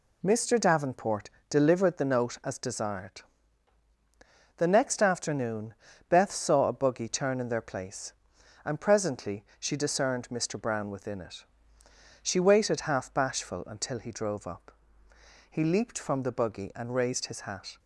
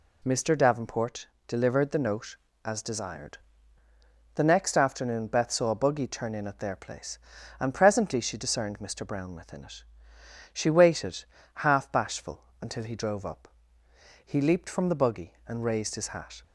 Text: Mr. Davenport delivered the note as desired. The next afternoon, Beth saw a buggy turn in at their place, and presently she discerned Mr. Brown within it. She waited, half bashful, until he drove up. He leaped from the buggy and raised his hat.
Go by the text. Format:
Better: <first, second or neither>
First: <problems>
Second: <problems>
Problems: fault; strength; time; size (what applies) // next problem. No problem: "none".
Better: second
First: pauses between "Davenport" and "delivered"; slight; at 1.3 s; 0.18 s long // skips "at"; at 7.4 s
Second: pauses between "Davenport" and "delivered"; slight; at 1.2 s; 0.22 s long